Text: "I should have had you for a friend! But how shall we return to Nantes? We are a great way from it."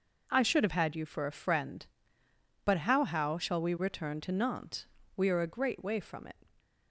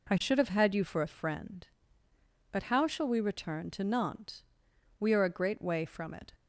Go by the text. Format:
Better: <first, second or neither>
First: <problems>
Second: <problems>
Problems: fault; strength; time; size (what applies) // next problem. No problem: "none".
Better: second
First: says "how" twice; at 3.0 s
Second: none